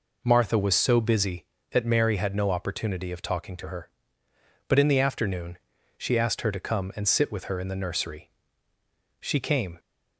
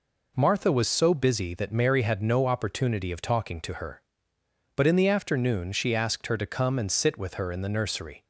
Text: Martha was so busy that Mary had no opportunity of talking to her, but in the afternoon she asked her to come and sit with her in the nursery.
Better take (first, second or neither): second